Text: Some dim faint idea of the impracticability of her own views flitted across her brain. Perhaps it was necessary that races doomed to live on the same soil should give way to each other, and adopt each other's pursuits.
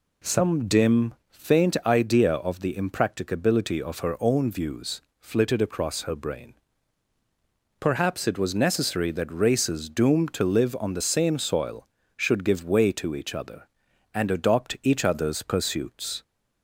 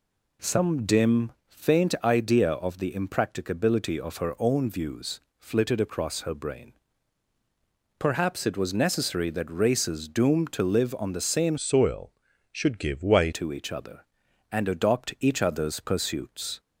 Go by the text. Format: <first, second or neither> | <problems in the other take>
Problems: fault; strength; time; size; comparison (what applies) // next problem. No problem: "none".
first | pauses between "dim" and "faint"; slight; at 1.3 s; 0.16 s long; slight in the first // pauses between "views" and "flitted"; slight; at 5.2 s; 0.18 s long; slight in the first // changes voice from "soil" to "way"; from 11.5 to 13.3 s; 1.8 s long